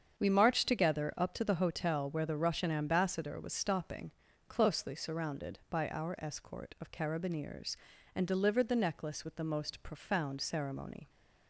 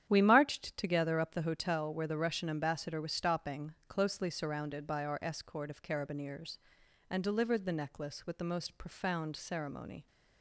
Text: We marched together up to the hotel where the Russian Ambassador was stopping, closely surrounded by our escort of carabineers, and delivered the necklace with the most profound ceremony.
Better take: first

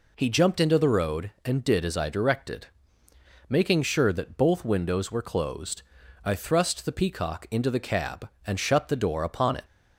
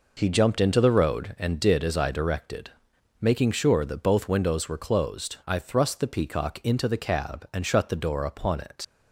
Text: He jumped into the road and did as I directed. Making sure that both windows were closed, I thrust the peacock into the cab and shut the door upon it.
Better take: first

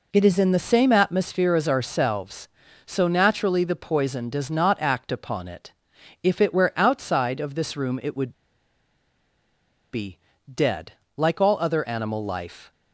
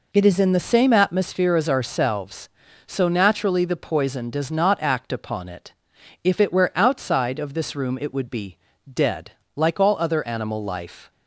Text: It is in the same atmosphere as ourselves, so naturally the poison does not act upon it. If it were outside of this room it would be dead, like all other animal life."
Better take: second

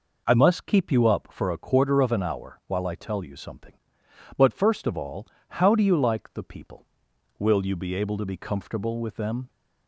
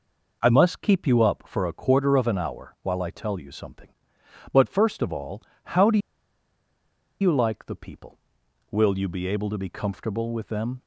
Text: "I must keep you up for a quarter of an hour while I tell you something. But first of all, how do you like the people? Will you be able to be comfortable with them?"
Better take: first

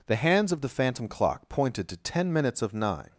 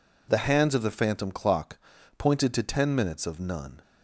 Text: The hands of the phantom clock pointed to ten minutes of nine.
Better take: first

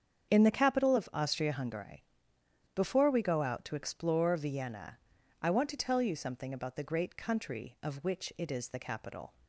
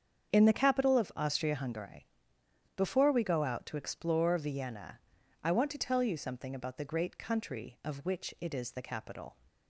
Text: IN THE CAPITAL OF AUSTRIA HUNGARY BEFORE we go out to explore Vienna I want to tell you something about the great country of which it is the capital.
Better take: neither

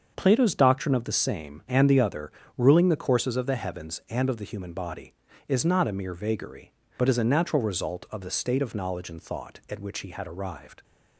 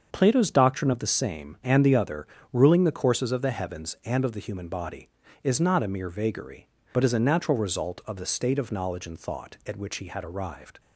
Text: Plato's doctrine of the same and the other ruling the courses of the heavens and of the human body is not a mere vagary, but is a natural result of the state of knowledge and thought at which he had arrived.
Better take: neither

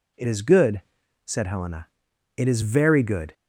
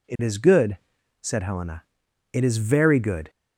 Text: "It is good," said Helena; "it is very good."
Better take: neither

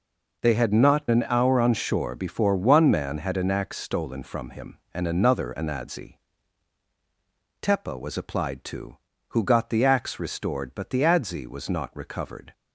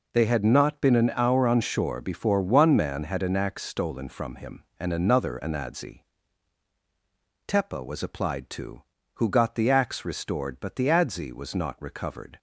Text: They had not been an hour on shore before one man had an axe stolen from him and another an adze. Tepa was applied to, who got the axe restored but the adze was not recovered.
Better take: second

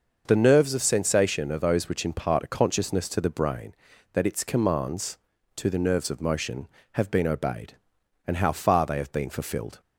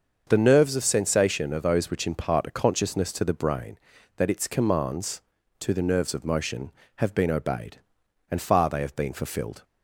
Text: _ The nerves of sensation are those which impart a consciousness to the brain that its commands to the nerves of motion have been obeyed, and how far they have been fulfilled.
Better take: first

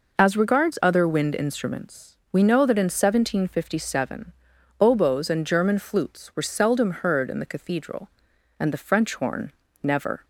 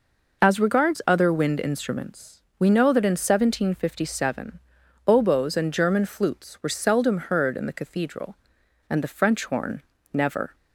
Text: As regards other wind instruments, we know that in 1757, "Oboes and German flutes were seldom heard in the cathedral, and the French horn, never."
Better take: neither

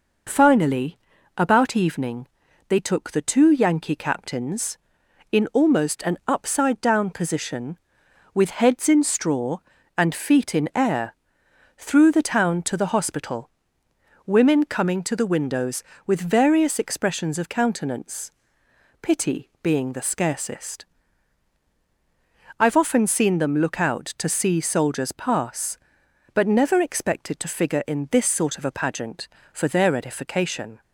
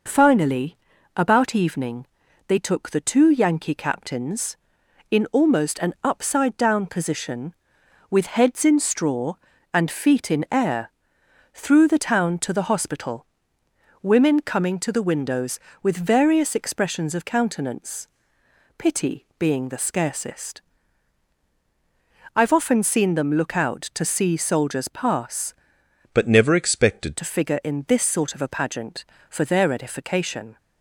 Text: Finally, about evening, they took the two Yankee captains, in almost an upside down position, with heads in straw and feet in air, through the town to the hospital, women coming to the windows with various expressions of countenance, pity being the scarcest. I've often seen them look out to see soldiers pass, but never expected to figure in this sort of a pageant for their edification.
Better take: first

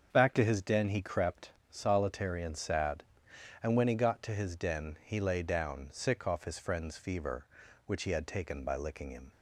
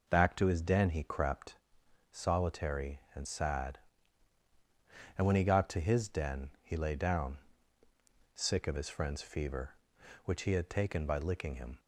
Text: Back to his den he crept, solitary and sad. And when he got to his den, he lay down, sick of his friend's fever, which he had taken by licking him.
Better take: second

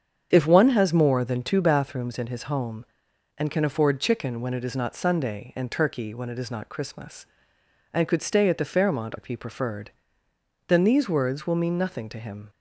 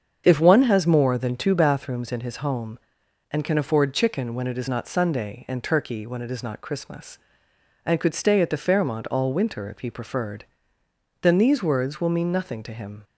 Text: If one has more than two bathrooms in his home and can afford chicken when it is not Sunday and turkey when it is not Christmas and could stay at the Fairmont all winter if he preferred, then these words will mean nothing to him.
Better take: second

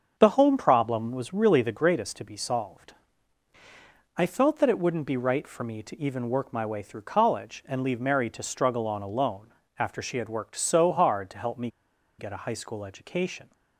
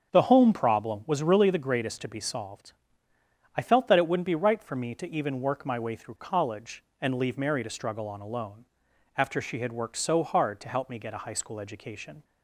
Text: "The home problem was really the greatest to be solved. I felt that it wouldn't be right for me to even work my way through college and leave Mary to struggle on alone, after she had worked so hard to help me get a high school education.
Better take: second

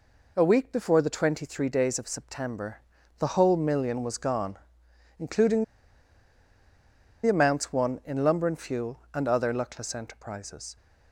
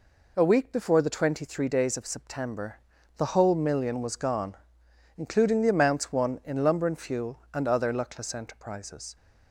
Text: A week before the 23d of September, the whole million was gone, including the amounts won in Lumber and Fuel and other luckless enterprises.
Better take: second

